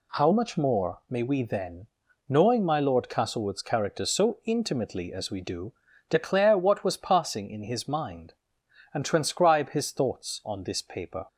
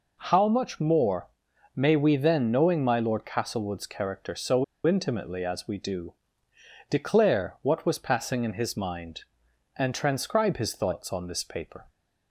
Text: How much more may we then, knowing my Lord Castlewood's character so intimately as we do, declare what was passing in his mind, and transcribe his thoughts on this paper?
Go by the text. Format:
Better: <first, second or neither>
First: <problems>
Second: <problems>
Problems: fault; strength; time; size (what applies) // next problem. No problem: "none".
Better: first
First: none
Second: pauses between "more" and "may"; noticeable; at 1.2 s; 0.46 s long // pauses between "so" and "intimately"; slight; at 4.6 s; 0.22 s long